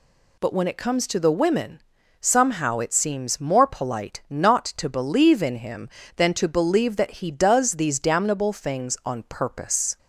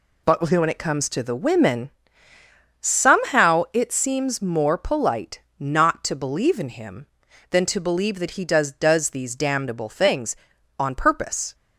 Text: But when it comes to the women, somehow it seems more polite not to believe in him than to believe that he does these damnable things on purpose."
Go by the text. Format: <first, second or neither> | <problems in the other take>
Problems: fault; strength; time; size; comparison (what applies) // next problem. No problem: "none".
first | pauses between "polite" and "not"; slight; at 5.4 s; 0.18 s long // says "does" twice; at 8.7 s